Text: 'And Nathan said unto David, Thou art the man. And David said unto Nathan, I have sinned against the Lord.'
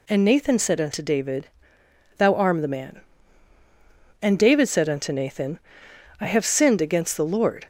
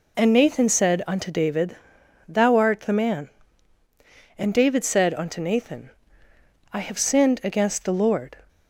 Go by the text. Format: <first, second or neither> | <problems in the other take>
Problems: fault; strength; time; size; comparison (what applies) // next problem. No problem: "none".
second | says "arm" for "art"; at 2.3 s